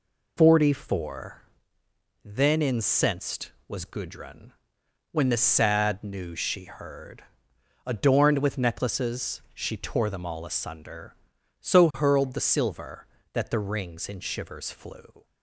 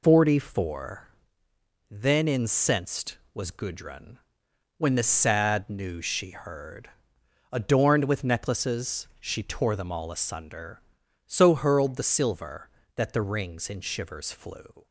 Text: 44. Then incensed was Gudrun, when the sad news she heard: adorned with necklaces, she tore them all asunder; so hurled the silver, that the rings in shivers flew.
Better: neither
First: none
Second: none

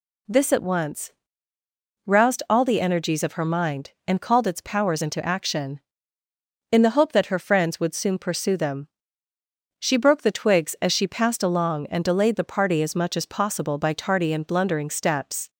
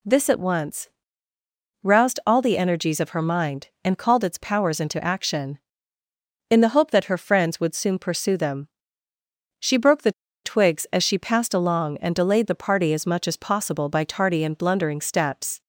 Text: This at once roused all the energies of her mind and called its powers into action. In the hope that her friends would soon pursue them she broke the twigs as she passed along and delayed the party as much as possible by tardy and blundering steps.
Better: first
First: pauses between "once" and "roused"; noticeable; at 1.1 s; 0.94 s long // pauses between "them" and "she"; noticeable; at 8.8 s; 0.94 s long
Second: pauses between "once" and "roused"; noticeable; at 0.8 s; 0.94 s long // pauses between "them" and "she"; noticeable; at 8.6 s; 0.94 s long // pauses between "the" and "twigs"; slight; at 10.1 s; 0.32 s long

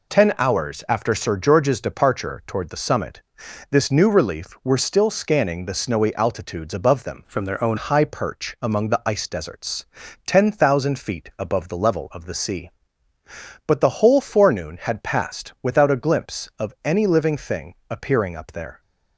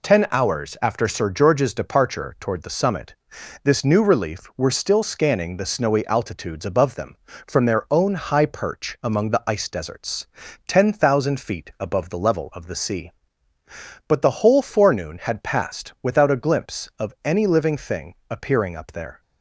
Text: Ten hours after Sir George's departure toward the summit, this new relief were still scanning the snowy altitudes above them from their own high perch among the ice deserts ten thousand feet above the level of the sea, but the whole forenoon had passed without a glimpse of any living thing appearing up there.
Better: second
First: changes voice from "from" to "own"; from 7.2 to 7.7 s; 0.5 s long // pauses between "deserts" and "ten"; at 9.8 s; 0.42 s long // pauses between "thing" and "appearing"; slight; at 17.7 s; 0.16 s long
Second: pauses between "deserts" and "ten"; at 10.2 s; 0.42 s long // pauses between "thing" and "appearing"; slight; at 18.1 s; 0.16 s long

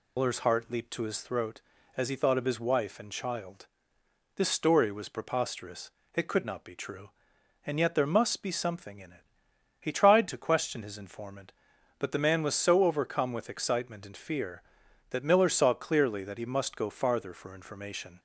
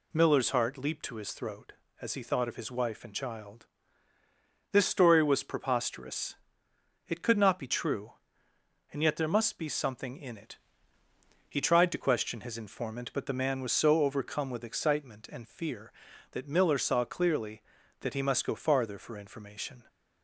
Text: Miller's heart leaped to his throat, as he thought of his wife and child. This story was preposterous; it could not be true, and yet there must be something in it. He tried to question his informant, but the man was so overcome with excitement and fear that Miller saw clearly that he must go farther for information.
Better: second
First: loses the start of "Miller's"; at 0.1 s; 100 ms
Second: none

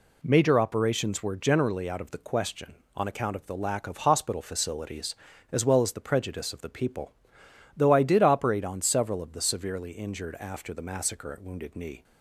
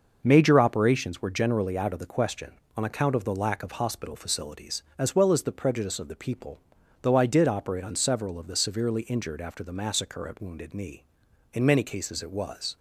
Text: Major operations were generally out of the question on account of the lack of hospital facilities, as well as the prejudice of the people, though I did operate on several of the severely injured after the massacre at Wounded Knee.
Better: first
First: none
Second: starts louder than the rest; noticeable; until 1.2 s; 6 dB // goes on to say "In many cases it was"; noticeable; from 11.5 s on; 1.2 s long

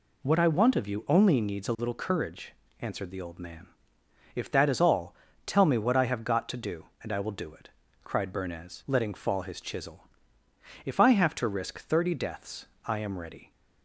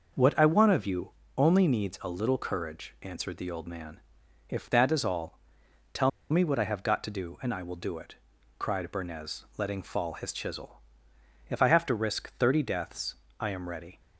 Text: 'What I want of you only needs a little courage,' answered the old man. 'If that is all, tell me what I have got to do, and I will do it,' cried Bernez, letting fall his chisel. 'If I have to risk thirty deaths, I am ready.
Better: first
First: none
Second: starts louder than the rest; noticeable; until 1.4 s; 6 dB // pauses between "you" and "only"; slight; at 1.0 s; 0.30 s long // pauses between "tell" and "me"; slight; at 6.0 s; 0.21 s long

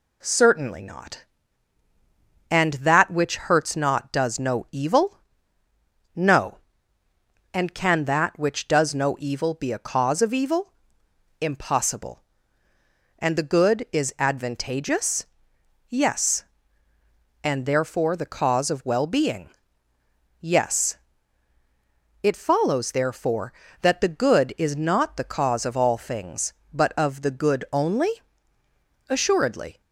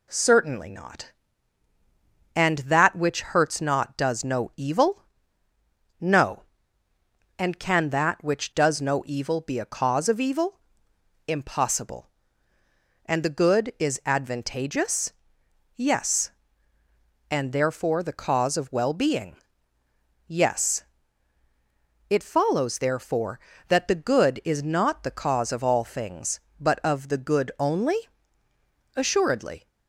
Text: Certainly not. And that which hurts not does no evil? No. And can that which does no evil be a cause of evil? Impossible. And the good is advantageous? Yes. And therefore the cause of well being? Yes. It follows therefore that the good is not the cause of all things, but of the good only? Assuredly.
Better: neither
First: none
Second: none

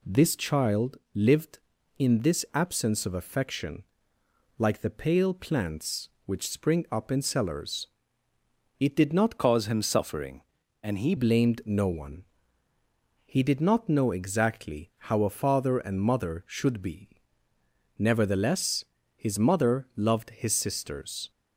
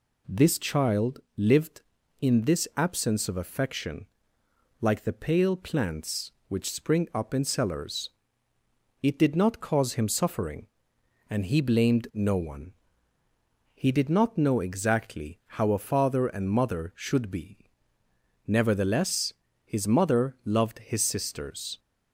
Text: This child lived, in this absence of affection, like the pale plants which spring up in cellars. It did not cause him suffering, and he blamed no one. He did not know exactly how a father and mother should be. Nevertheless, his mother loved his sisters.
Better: second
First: pauses between "child" and "lived"; slight; at 0.9 s; 0.16 s long // changes voice from "cause" to "he"; from 9.3 to 11.1 s; 1.8 s long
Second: pauses between "child" and "lived"; slight; at 1.2 s; 0.16 s long

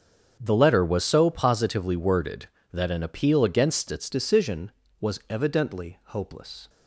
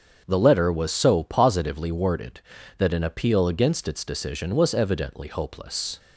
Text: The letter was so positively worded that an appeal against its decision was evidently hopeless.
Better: second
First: starts louder than the rest; strong; until 1.4 s; 7.5 dB // changes voice at "decision"; from 4.0 s on; 2.6 s long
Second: starts louder than the rest; strong; until 1.2 s; 7 dB

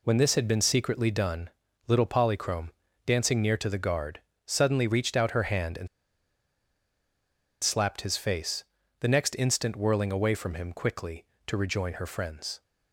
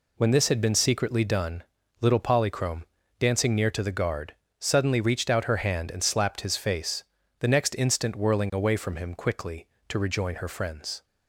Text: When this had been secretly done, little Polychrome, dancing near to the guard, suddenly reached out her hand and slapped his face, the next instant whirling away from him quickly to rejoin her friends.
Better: second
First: pauses between "and" and "slapped"; strong; at 5.8 s; 1.7 s long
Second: none

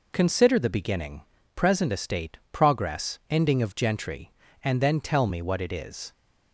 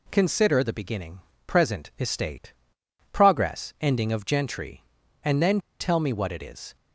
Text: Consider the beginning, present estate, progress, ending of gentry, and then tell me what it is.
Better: first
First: none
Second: pauses between "then" and "tell"; slight; at 5.5 s; 0.20 s long

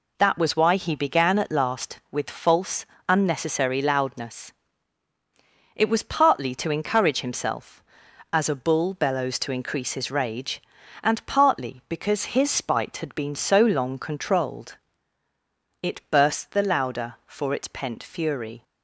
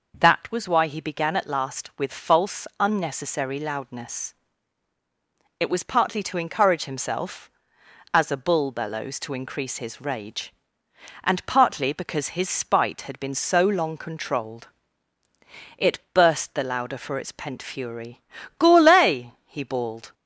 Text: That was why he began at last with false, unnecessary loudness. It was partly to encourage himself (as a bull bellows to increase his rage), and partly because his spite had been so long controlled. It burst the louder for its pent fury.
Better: first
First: none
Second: goes on to say "Gourlay he bawled"; from 18.5 s on; 1.5 s long

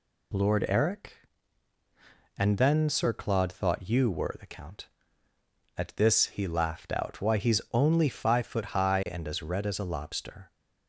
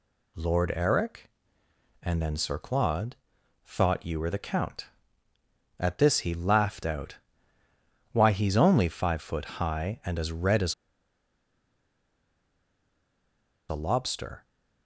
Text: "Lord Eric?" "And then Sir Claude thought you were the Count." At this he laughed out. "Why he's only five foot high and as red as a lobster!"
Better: first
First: none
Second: pauses between "Claude" and "thought"; noticeable; at 3.1 s; 0.48 s long // pauses between "as" and "a"; strong; at 10.7 s; 2.9 s long

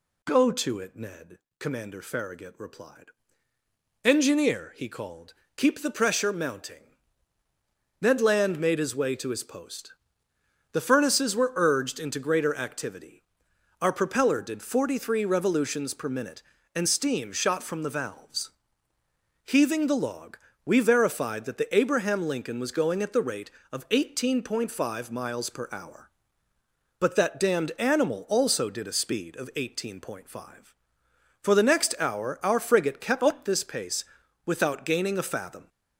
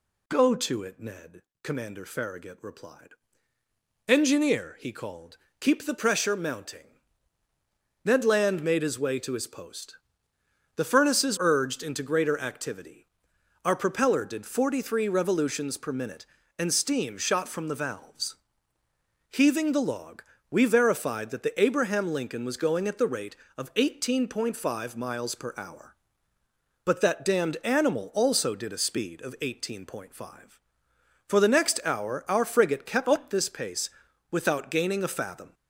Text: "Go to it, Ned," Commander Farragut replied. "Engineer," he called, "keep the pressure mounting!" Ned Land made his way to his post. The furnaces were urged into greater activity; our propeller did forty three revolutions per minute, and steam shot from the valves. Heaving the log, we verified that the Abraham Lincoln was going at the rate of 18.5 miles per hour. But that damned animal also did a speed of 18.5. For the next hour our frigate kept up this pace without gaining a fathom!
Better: first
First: pauses between "pace" and "without"; at 34.0 s; 0.40 s long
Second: skips "were"; at 11.3 s // pauses between "pace" and "without"; at 33.8 s; 0.40 s long

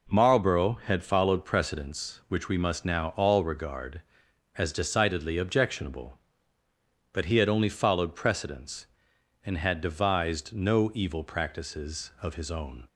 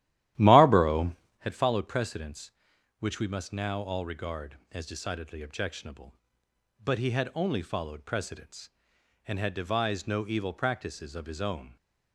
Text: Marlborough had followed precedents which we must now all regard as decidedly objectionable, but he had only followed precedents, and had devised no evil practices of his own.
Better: first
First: none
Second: starts louder than the rest; strong; until 1.5 s; 13.5 dB

